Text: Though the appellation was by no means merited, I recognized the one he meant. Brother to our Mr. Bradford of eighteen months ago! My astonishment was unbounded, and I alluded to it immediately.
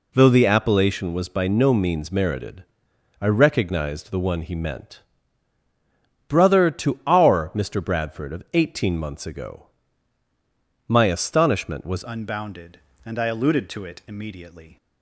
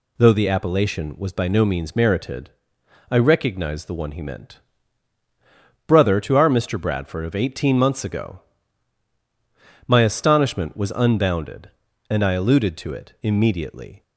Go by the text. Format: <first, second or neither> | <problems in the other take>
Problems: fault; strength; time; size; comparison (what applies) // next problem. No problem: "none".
second | changes voice at "unbounded"; from 12.0 s on; 2.7 s long